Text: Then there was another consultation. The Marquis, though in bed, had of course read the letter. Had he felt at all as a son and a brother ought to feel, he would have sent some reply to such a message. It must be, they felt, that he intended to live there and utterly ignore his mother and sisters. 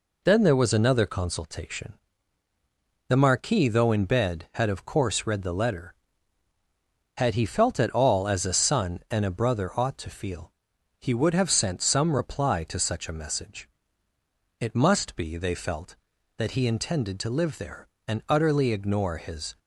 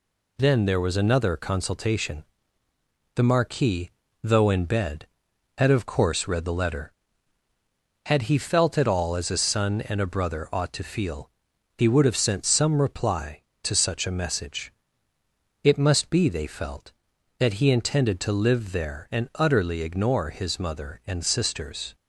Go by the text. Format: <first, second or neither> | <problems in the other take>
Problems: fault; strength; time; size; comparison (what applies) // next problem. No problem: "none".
second | stops before "mother and sisters"; at 19.5 s